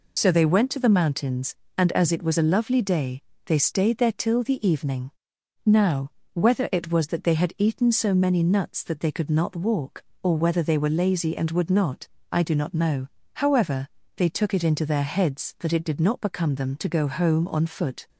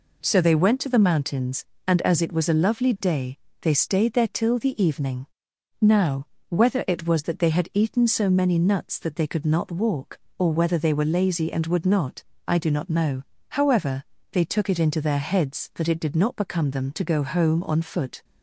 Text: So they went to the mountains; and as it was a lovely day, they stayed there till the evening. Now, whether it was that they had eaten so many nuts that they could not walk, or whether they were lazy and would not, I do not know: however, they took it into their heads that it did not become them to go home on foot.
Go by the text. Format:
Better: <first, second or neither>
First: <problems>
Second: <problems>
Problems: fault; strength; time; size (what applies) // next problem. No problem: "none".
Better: second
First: loses the start of "So"; at 0.1 s; 50 ms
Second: none